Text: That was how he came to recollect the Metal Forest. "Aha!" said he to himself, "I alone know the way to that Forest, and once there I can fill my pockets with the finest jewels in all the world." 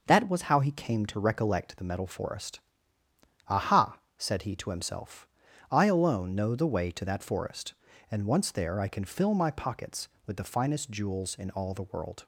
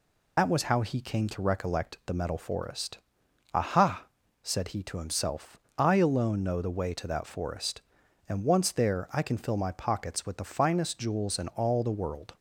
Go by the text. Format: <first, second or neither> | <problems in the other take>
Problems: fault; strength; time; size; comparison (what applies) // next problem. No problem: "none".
first | loses the start of "That"; at 0.3 s; 70 ms